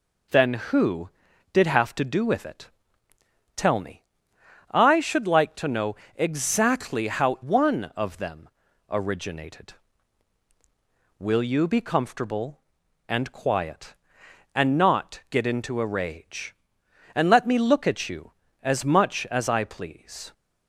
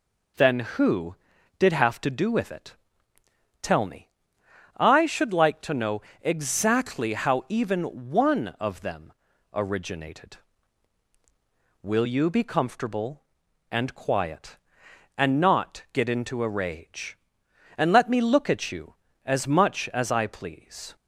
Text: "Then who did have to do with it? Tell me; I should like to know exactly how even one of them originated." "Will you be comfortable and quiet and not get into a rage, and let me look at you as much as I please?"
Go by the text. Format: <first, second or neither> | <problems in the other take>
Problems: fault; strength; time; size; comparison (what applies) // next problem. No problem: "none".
second | pauses between "know" and "exactly"; slight; at 5.9 s; 0.22 s long; slight in the second // skips "even"; at 7.4 s // pauses between "them" and "originated"; at 8.4 s; 0.40 s long; also in the second